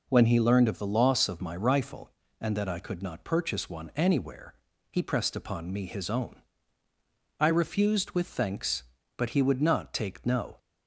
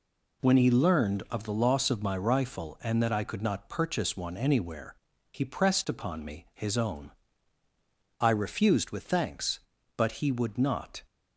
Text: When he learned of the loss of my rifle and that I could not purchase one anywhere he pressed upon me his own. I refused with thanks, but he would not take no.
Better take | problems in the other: first | pauses between "anywhere" and "he"; at 4.9 s; 0.38 s long; slight in the first // stops before "take no"; at 11.0 s

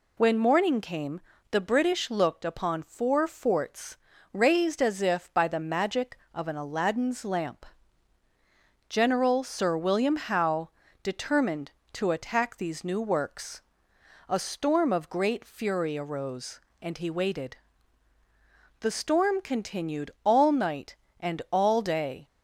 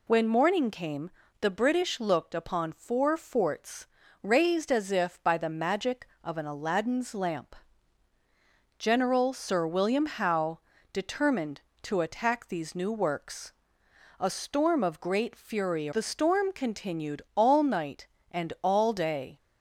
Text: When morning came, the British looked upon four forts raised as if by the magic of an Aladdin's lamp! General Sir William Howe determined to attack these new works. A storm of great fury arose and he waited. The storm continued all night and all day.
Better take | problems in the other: first | pauses between "forts" and "raised"; slight; at 3.8 s; 0.36 s long; slight in the first // pauses between "Howe" and "determined"; slight; at 10.5 s; 0.34 s long; slight in the first // skips "arose and he waited"; at 15.9 s

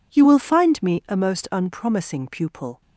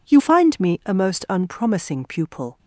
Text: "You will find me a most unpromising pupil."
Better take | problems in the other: first | skips "will"; at 0.1 s

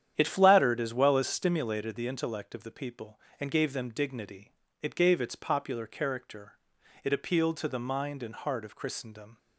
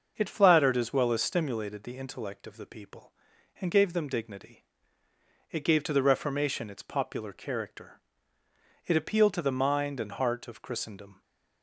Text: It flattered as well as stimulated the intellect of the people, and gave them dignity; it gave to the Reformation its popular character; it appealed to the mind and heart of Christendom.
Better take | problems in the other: second | starts louder than the rest; strong; until 1.1 s; 9.5 dB; also in the second // skips "to the Reformation"; at 5.1 s

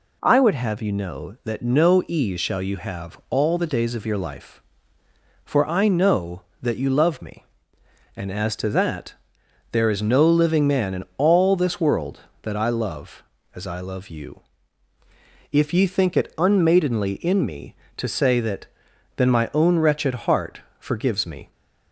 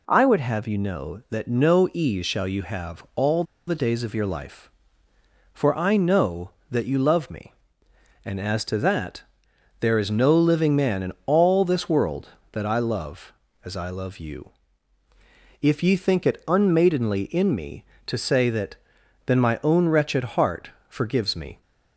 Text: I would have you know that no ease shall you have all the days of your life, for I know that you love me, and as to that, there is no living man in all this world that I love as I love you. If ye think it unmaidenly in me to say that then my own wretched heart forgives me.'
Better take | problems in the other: first | pauses between "all" and "the"; slight; at 3.4 s; 0.24 s long // pauses between "that" and "then"; noticeable; at 18.7 s; 0.52 s long; noticeable in the first // pauses between "heart" and "forgives"; slight; at 20.7 s; 0.18 s long; slight in the first

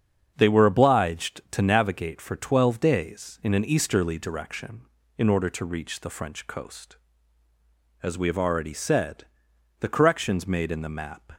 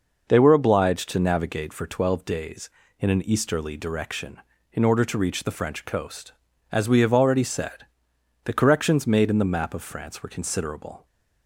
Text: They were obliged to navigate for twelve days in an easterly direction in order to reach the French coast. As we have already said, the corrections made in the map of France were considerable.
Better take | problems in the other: second | starts louder than the rest; strong; until 1.3 s; 7.5 dB // stops before "of France were considerable"; at 11.3 s

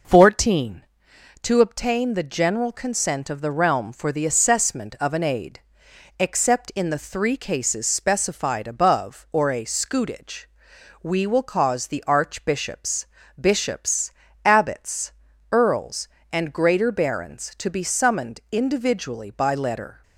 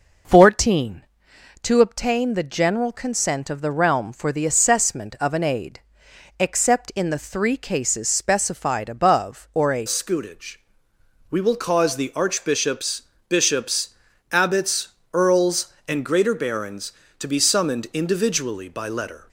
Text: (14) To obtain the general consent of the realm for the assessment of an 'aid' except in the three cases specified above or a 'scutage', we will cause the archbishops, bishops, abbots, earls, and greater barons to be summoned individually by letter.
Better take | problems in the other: first | pauses between "aid" and "except"; noticeable; at 5.7 s; 0.62 s long; noticeable in the first // changes voice at "scutage"; from 9.8 s on; 9.4 s long

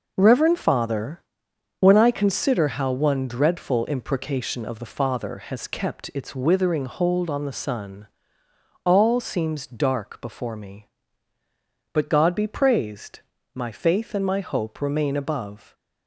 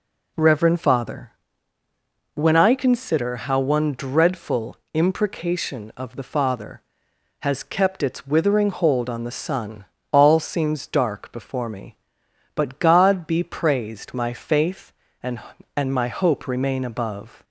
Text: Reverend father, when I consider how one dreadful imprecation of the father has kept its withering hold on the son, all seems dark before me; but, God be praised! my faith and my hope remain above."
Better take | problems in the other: first | pauses between "dreadful" and "imprecation"; slight; at 4.7 s; 0.16 s long // says "and" twice; at 15.7 s

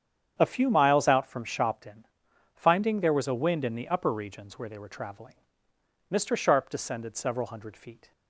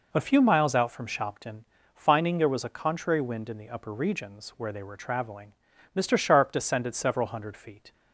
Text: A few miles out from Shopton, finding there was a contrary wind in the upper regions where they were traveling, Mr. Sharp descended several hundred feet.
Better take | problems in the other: second | starts louder than the rest; strong; until 1.4 s; 8 dB // skips "contrary"; at 3.3 s

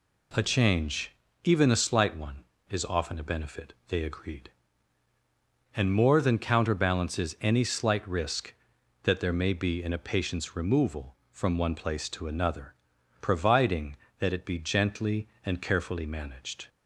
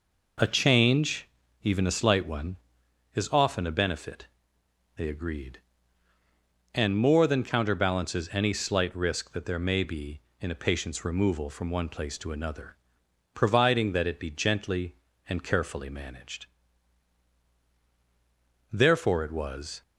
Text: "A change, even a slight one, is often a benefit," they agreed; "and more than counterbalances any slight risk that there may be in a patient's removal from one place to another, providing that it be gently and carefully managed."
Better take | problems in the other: first | goes on to say "Therefore it was"; noticeable; from 18.6 s on; 1.1 s long

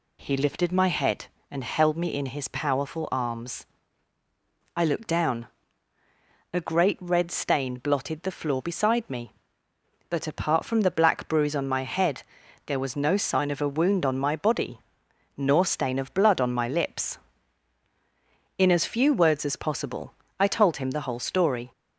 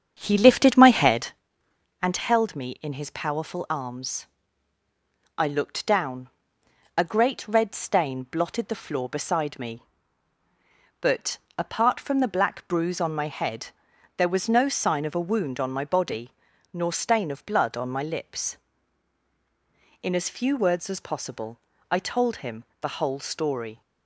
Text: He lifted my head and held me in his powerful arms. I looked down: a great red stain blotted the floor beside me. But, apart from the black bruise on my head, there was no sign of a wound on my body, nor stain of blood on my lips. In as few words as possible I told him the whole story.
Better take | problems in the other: first | starts louder than the rest; strong; until 1.4 s; 8 dB // pauses between "possible" and "I"; slight; at 21.5 s; 0.32 s long; slight in the first // pauses between "him" and "the"; slight; at 22.6 s; 0.16 s long

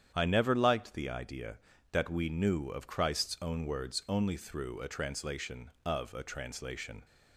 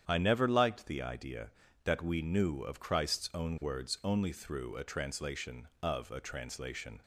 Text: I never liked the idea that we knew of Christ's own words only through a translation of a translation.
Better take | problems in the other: neither | starts louder than the rest; strong; the same in both

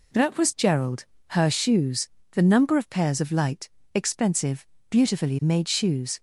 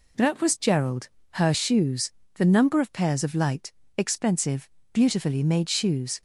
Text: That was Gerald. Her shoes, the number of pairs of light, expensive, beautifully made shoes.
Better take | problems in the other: neither | none

